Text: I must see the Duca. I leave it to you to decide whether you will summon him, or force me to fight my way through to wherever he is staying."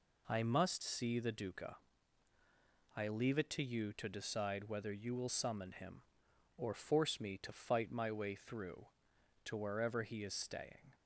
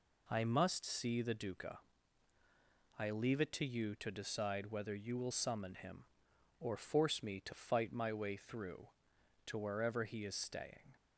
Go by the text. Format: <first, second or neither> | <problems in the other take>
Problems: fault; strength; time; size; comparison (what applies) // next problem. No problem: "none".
neither | none